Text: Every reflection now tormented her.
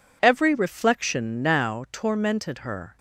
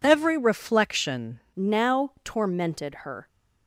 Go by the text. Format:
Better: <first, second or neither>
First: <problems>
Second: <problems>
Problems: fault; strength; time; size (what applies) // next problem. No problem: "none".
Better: first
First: none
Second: changes voice at "now"; from 1.5 s on; 1.7 s long